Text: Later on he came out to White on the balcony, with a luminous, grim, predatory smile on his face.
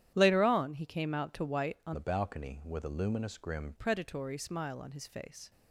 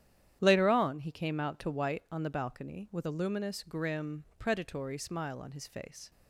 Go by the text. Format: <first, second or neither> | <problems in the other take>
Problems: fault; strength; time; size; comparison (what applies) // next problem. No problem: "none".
second | starts louder than the rest; strong; until 1.1 s; 11 dB; strong in the second // changes voice from "the" to "grim"; from 1.9 to 3.7 s; 1.8 s long